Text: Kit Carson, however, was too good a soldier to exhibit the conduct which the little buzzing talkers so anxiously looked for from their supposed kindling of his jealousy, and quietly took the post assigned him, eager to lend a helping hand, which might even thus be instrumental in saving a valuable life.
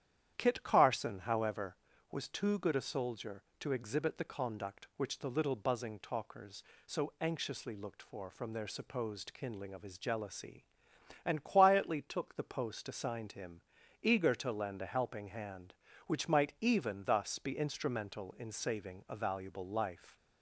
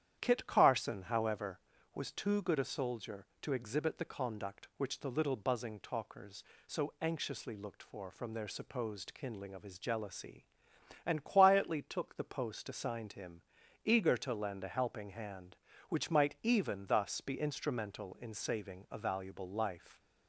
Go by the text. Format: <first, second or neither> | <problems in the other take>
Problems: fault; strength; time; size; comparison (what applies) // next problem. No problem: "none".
neither | starts louder than the rest; strong; the same in both